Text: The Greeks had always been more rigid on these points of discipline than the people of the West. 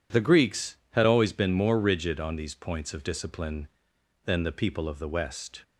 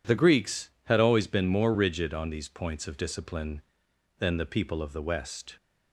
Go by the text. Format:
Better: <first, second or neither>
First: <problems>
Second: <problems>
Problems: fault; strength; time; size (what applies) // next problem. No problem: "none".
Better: neither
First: none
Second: none